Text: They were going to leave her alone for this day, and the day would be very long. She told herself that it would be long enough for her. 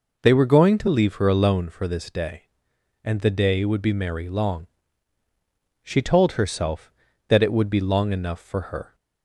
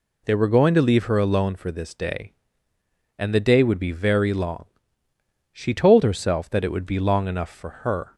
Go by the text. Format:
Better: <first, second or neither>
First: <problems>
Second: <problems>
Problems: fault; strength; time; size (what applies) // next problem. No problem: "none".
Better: second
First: says "merry" for "very"; at 3.9 s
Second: none